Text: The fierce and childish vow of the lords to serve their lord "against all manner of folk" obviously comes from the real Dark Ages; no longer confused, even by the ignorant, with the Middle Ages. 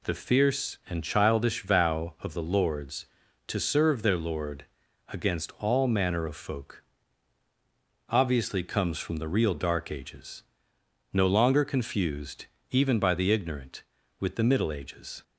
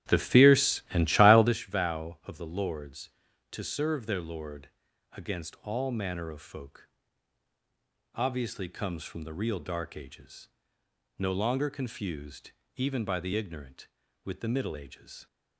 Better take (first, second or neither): first